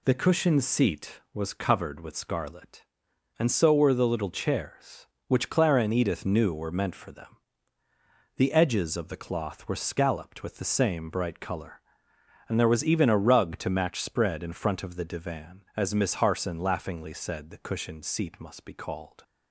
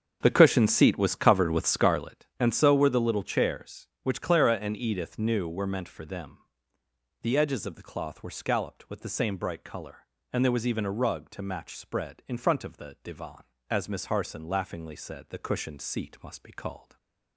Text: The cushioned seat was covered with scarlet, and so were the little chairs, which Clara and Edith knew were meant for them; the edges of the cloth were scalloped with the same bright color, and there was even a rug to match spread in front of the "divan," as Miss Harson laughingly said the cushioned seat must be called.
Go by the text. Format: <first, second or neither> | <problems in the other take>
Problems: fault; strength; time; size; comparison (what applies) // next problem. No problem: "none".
first | starts louder than the rest; until 2.0 s; 7 dB // stays silent after the last word; slight; from 16.7 s on; 0.6 s long